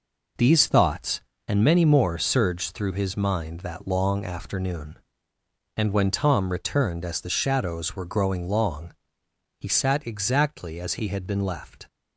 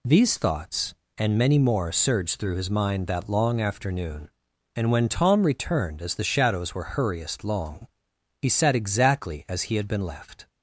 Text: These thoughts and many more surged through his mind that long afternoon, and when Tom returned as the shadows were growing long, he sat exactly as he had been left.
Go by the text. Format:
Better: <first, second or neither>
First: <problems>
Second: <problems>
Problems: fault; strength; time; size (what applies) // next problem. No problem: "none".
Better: first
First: none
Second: says "hurriest" for "growing"; at 6.9 s